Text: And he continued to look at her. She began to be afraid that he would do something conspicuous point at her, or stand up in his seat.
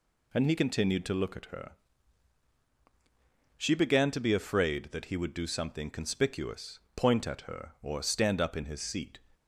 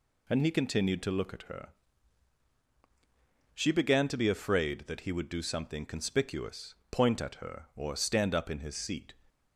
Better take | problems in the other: neither | pauses between "conspicuous" and "point"; slight; the same in both

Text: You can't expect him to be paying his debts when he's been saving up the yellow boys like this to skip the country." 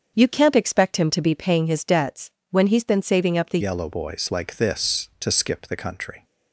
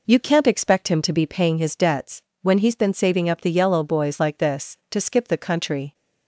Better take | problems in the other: second | starts louder than the rest; until 1.1 s; 7 dB // pauses between "debts" and "when"; slight; at 2.2 s; 0.22 s long; slight in the second // changes voice at "yellow"; from 3.6 s on; 2.6 s long

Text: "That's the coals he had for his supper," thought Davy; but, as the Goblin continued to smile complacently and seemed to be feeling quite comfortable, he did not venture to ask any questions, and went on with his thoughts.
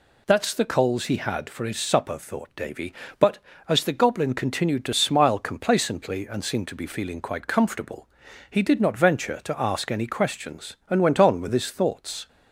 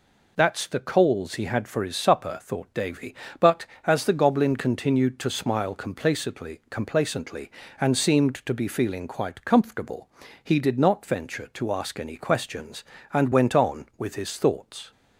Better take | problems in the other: first | says "complacently" twice; at 6.6 s

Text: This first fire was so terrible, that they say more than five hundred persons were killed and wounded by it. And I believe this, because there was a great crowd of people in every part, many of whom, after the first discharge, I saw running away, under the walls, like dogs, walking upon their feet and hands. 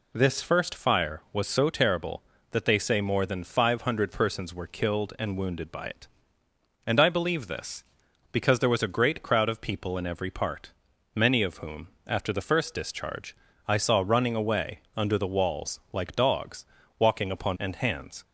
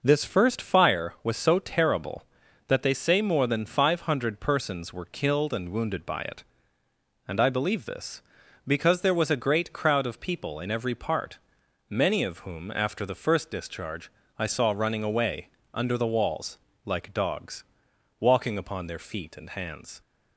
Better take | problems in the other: second | skips "their feet"; at 17.5 s

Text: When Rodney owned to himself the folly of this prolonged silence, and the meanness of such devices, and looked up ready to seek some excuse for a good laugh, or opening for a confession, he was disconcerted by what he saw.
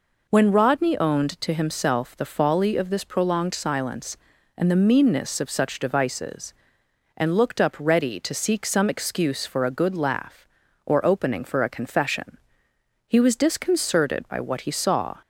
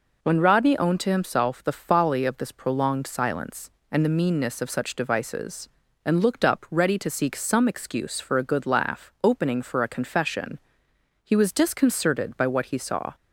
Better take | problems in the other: first | skips "or"; at 9.1 s

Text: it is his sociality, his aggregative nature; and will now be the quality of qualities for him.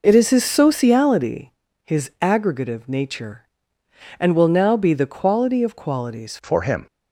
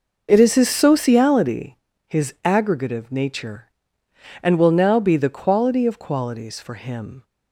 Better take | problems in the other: second | changes voice at "for"; from 6.4 s on; 0.4 s long

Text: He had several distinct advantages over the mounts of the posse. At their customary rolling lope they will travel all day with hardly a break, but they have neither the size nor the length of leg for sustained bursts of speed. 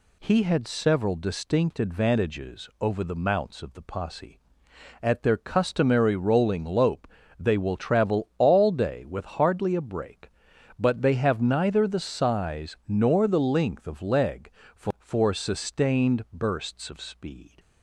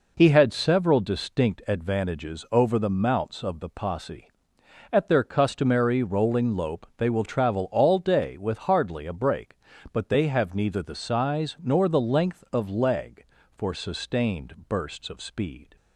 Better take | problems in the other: second | pauses between "lope" and "they"; slight; at 7.0 s; 0.32 s long // says "for" twice; at 14.9 s

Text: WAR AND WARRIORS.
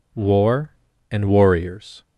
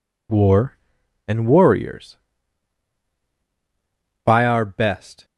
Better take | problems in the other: first | goes on to say "By our best"; noticeable; from 4.2 s on; 1.0 s long

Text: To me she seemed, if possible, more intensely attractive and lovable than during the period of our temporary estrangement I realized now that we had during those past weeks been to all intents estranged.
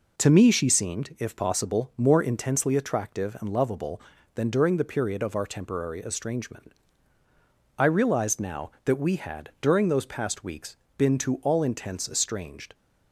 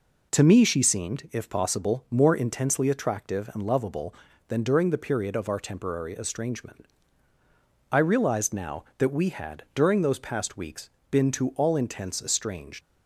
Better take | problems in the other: first | pauses between "estrangement" and "I"; at 6.8 s; 1.0 s long; also in the first // pauses between "weeks" and "been"; slight; at 10.9 s; 0.18 s long; slight in the first // leaves "estranged" unfinished; at 12.8 s; 60 ms

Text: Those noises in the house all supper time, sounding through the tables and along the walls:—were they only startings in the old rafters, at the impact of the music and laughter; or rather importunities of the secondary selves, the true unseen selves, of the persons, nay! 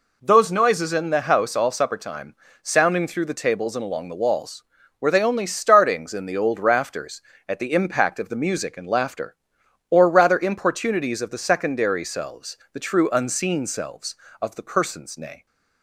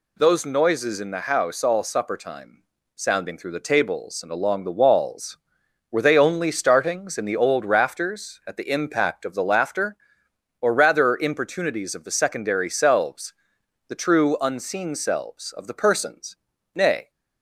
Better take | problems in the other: first | skips "music and"; at 9.4 s

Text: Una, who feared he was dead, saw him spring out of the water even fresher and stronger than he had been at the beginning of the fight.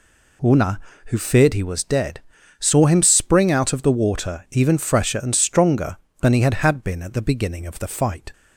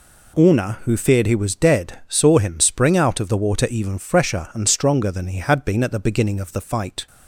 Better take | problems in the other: second | says "had" twice; at 6.5 s

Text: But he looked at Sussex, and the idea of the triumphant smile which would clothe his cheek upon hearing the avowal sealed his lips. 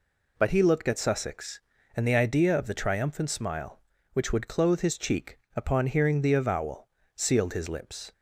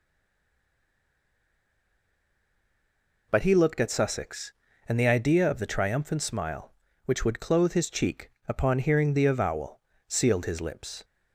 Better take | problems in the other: first | stays silent before the first word; strong; until 3.2 s; 3.2 s long // pauses between "cheek" and "upon"; slight; at 8.2 s; 0.18 s long; slight in the first // pauses between "avowal" and "sealed"; slight; at 9.7 s; 0.28 s long; slight in the first

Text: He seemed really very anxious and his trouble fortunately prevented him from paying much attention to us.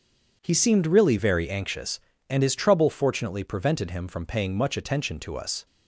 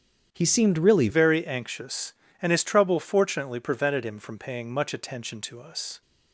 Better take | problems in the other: first | starts louder than the rest; strong; until 1.3 s; 8.5 dB // changes voice at "very"; from 1.0 s on; 5.0 s long

